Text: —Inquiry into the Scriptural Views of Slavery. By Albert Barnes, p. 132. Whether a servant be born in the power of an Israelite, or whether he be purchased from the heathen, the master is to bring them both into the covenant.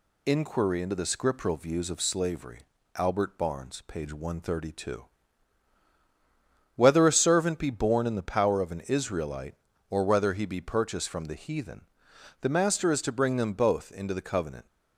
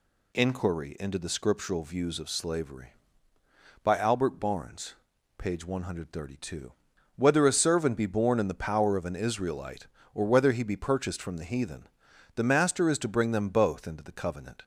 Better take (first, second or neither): second